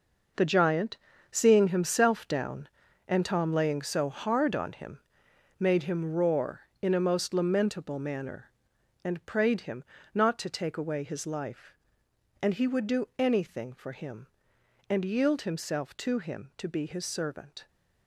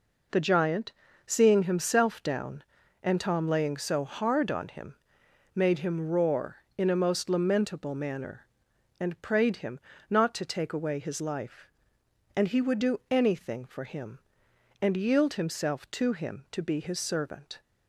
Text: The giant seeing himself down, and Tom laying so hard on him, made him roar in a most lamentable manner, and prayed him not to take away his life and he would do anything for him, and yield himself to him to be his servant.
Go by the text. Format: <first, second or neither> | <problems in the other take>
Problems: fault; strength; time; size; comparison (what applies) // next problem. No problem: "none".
second | gets quieter; strong; throughout; 11 dB // pauses between "giant" and "seeing"; slight; at 0.9 s; 0.34 s long; slight in the second // pauses between "him" and "not"; slight; at 9.8 s; 0.28 s long; slight in the second